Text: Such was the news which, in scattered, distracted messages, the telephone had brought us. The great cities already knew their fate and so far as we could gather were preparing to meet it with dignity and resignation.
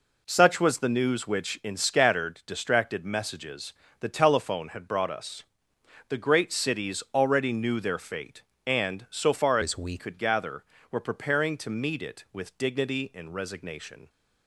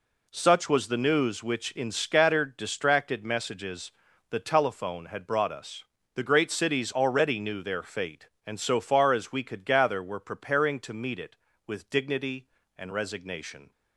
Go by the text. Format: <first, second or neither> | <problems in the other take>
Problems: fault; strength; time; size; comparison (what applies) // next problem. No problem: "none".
second | changes voice from "as" to "we"; from 9.6 to 9.9 s; 0.3 s long